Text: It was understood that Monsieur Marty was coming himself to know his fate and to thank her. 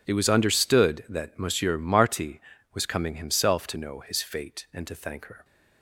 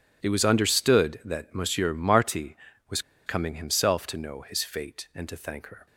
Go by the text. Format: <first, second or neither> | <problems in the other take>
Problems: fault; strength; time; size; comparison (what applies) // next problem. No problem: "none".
first | pauses between "was" and "coming"; slight; at 3.0 s; 0.25 s long